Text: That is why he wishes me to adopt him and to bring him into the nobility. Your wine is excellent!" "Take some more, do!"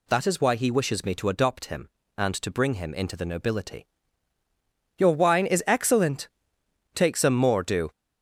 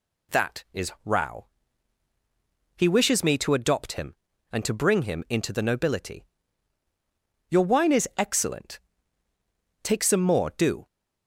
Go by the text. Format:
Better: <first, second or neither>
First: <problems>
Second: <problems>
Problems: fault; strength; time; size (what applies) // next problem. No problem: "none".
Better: first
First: none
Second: says "rao" for "why"; at 1.0 s